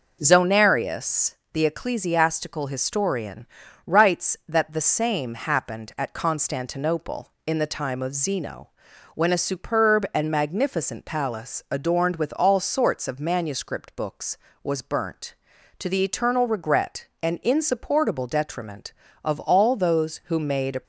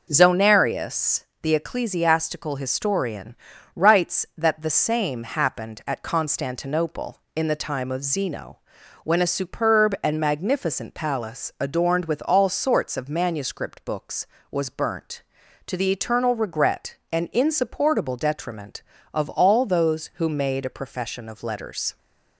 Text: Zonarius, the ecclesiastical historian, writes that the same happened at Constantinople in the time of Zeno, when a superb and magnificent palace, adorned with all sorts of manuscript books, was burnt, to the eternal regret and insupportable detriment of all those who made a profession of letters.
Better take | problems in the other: second | stops before "profession of letters"; at 20.8 s

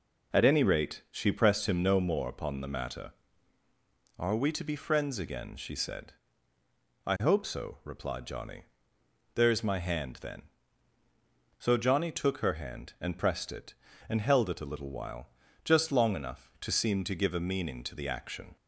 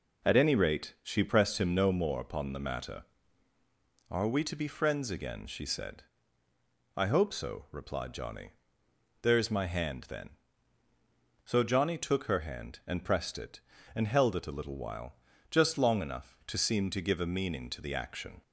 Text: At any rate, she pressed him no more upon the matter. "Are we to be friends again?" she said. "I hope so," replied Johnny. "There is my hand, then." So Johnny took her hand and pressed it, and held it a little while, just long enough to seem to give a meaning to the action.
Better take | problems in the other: neither | none

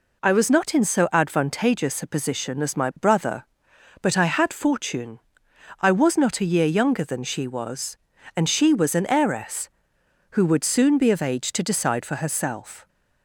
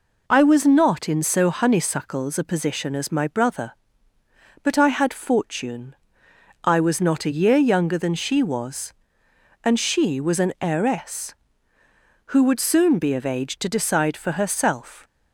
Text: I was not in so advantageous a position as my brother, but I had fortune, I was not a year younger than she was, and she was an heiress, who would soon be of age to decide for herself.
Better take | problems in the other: first | says "honeysuckles" for "advantageous"; at 1.4 s

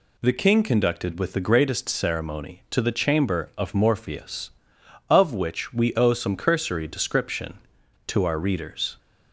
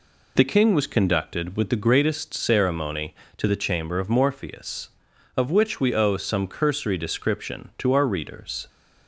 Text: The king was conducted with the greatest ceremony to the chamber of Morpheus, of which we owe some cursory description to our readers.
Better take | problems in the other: second | skips "was"; at 0.6 s

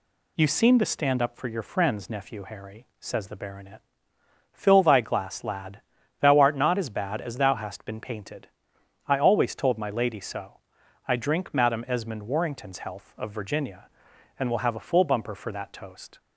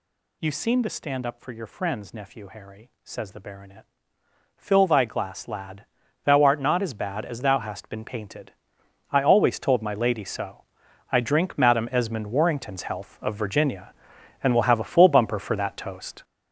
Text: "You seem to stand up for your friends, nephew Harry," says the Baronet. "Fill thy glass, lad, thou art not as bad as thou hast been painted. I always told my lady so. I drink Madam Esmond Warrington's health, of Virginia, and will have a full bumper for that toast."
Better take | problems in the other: first | gets louder; strong; throughout; 8 dB

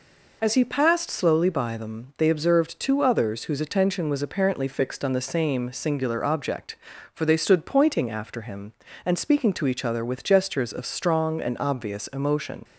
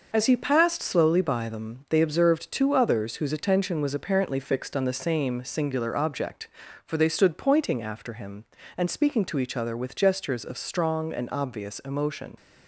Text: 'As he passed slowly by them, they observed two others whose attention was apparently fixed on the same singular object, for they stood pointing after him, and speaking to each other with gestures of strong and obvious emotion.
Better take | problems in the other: first | gets quieter; noticeable; throughout; 5 dB

